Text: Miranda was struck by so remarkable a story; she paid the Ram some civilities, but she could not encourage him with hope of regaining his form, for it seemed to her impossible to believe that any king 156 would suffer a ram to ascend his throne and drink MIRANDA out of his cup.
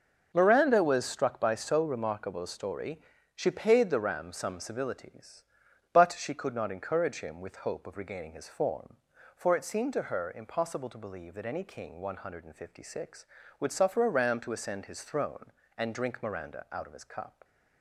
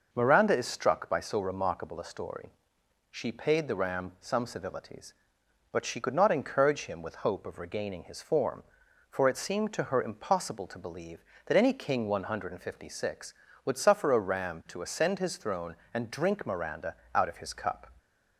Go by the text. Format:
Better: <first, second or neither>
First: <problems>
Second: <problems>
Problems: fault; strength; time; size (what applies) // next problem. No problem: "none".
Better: first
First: none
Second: says "is" for "was"; at 0.5 s // pauses between "MIRANDA" and "out"; slight; at 16.9 s; 0.22 s long